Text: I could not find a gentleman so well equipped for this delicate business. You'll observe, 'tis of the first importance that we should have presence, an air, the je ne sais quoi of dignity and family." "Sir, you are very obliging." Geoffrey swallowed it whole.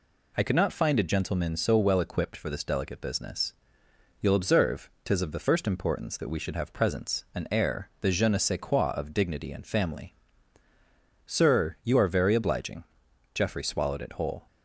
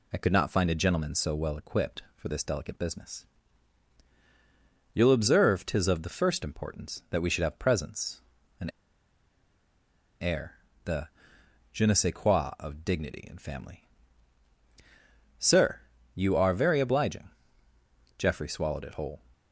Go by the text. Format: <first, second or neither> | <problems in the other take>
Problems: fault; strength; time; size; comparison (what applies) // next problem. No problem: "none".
first | pauses between "an" and "air"; strong; at 8.6 s; 1.5 s long // pauses between "the" and "je"; noticeable; at 11.0 s; 0.64 s long